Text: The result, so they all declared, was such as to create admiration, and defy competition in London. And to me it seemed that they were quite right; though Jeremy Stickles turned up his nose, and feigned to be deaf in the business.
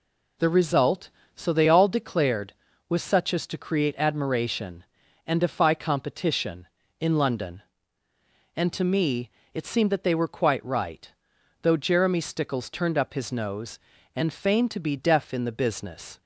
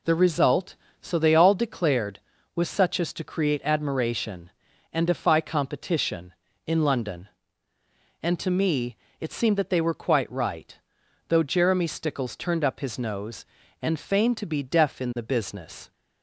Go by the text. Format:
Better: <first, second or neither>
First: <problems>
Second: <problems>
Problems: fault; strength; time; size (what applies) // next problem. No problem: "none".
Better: neither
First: pauses between "me" and "it"; slight; at 9.3 s; 0.24 s long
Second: pauses between "me" and "it"; slight; at 8.9 s; 0.24 s long